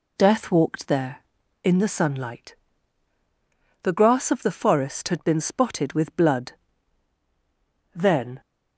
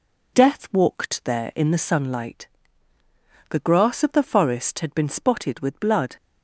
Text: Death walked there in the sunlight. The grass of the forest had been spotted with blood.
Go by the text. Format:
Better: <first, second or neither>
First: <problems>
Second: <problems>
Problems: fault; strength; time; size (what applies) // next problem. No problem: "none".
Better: second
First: goes on to say "Then"; slight; from 7.9 s on; 0.46 s long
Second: none